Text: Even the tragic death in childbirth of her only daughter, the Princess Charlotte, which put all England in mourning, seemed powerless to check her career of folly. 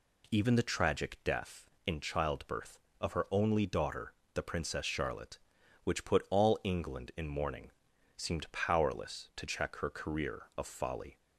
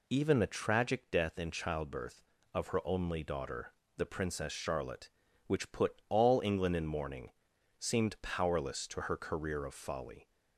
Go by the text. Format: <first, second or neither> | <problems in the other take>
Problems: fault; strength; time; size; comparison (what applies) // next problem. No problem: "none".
first | skips "check"; at 9.0 s